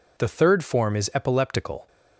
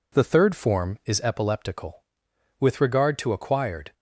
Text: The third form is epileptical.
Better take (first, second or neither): first